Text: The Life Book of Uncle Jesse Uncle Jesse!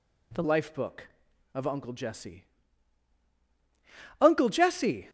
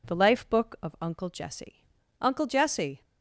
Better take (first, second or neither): second